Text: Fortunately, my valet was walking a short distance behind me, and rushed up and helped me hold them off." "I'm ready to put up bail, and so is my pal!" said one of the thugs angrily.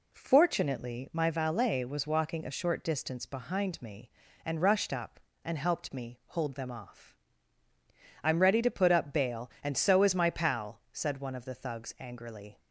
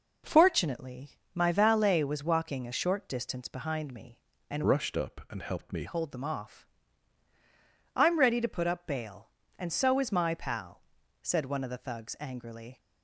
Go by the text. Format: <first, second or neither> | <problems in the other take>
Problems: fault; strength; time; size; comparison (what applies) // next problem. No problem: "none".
first | changes voice from "rushed" to "me"; from 4.6 to 5.8 s; 1.2 s long